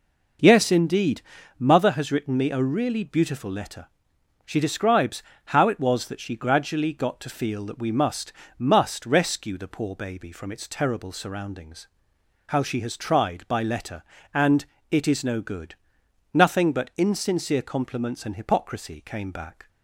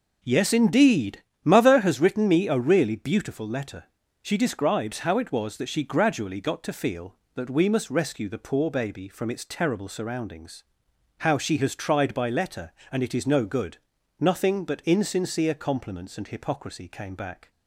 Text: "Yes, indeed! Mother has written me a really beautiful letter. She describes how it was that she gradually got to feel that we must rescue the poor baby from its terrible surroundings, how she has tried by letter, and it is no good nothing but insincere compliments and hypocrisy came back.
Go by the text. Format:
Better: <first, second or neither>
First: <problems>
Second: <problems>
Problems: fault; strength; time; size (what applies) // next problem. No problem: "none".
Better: second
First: pauses between "describes" and "how"; slight; at 5.2 s; 0.24 s long // says "must" twice; at 8.5 s // pauses between "and" and "it"; slight; at 14.6 s; 0.26 s long // pauses between "good" and "nothing"; noticeable; at 15.7 s; 0.58 s long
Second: pauses between "good" and "nothing"; at 13.7 s; 0.42 s long